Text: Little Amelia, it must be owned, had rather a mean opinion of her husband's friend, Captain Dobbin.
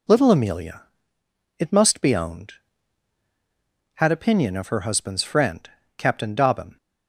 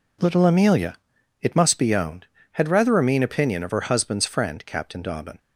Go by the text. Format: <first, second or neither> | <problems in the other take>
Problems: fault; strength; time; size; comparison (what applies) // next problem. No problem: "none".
second | skips "rather a mean"; at 4.1 s